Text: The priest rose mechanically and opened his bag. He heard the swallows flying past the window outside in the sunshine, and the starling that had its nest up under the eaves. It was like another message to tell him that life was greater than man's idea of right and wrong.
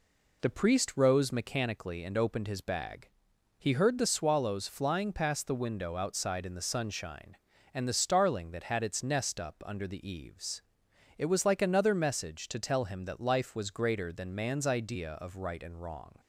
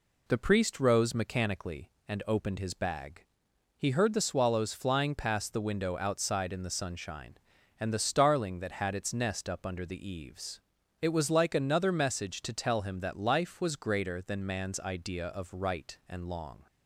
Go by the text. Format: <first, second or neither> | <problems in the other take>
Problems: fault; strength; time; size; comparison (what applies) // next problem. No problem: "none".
first | says "long" for "wrong"; at 16.2 s